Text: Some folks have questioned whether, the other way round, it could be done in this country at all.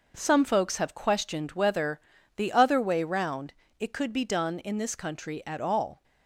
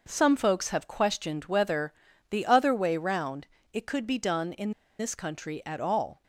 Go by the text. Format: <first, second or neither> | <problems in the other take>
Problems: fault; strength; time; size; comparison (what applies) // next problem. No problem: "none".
first | pauses between "in" and "this"; slight; at 4.7 s; 0.28 s long